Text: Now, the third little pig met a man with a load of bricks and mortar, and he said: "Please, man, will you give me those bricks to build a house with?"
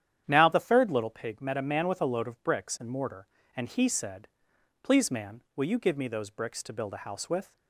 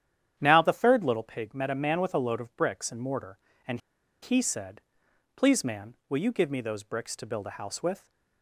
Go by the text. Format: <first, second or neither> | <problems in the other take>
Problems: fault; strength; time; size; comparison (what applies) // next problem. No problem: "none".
first | starts louder than the rest; strong; until 1.3 s; 10 dB; strong in the first // pauses between "and" and "he"; at 3.7 s; 0.43 s long